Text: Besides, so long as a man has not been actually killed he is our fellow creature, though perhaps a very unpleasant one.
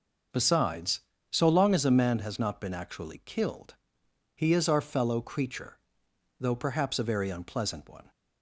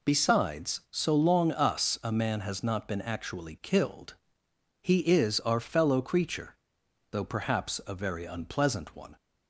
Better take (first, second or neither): first